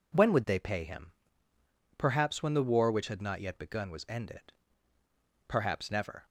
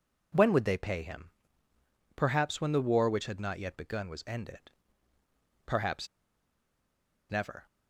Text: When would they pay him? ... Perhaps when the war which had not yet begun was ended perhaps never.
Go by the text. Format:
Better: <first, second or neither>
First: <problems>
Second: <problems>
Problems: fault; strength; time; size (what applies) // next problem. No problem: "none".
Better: first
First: pauses between "ended" and "perhaps"; noticeable; at 4.5 s; 0.94 s long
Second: pauses between "ended" and "perhaps"; noticeable; at 4.7 s; 0.94 s long // pauses between "perhaps" and "never"; at 6.0 s; 1.2 s long